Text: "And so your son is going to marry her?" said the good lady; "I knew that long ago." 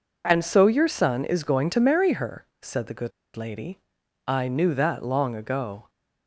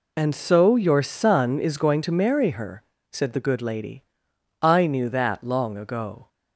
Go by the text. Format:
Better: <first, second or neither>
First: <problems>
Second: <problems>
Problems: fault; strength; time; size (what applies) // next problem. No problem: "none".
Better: second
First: pauses between "good" and "lady"; slight; at 3.1 s; 0.26 s long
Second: none